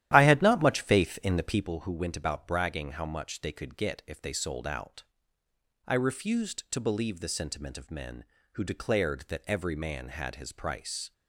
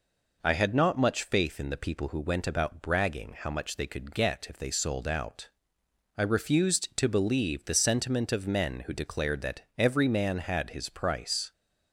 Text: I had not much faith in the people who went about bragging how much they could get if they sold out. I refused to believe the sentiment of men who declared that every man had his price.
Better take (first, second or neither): second